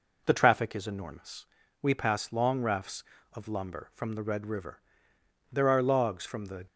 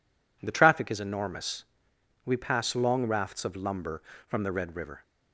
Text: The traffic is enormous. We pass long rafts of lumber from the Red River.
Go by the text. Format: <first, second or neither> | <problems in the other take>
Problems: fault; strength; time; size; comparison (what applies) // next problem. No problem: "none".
second | goes on to say "There are logs from the"; noticeable; from 5.5 s on; 1.1 s long